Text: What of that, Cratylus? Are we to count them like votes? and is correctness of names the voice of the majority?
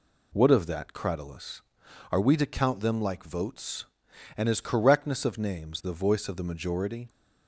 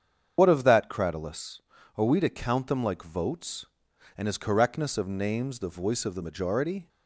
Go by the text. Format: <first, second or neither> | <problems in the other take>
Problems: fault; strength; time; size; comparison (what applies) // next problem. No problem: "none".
first | loses the start of "What"; at 0.3 s; 85 ms // starts louder than the rest; strong; until 1.3 s; 7.5 dB